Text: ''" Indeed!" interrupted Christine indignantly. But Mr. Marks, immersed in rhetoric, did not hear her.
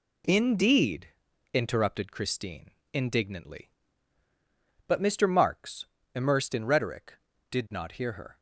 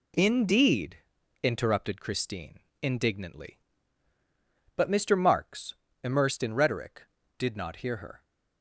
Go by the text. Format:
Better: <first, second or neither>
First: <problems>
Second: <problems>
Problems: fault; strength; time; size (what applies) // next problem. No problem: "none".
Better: neither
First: pauses between "Christine" and "indignantly"; slight; at 2.7 s; 0.22 s long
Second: pauses between "Christine" and "indignantly"; slight; at 2.6 s; 0.22 s long